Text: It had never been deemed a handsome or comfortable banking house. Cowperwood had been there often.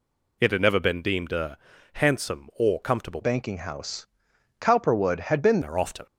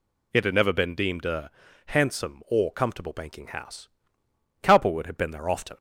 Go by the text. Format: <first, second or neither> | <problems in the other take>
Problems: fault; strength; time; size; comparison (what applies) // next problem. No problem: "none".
second | pauses between "a" and "handsome"; at 1.5 s; 0.38 s long; also in the second // changes voice from "banking" to "been"; from 3.2 to 5.6 s; 2.4 s long